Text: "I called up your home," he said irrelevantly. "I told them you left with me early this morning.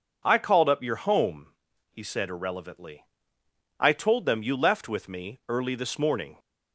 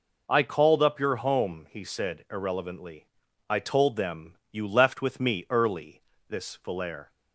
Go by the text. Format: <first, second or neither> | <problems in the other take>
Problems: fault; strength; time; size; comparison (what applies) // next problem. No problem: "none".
first | pauses between "early" and "this"; slight; at 6.0 s; 0.28 s long // says "valere" for "morning"; at 6.6 s